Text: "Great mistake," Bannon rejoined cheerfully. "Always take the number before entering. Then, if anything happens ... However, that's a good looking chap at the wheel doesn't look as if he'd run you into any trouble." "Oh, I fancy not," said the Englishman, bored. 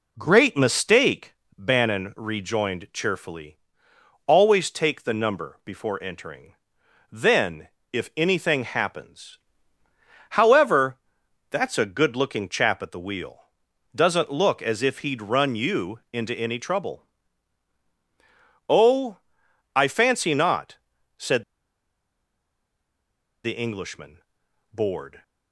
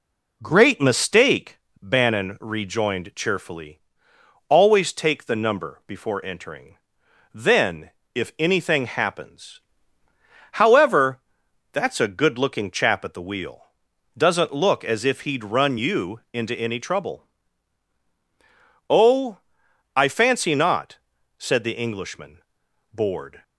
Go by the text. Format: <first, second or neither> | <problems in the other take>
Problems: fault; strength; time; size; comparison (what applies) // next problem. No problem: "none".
second | pauses between "wheel" and "doesn't"; noticeable; at 13.4 s; 0.52 s long; noticeable in the second // pauses between "said" and "the"; strong; at 21.4 s; 2.0 s long